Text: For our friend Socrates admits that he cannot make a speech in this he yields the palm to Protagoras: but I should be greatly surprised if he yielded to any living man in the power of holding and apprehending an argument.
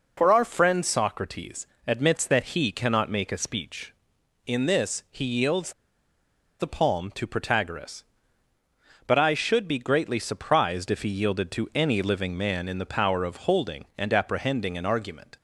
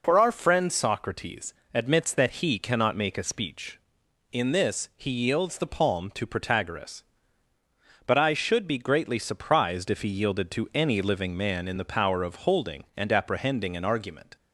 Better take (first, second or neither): second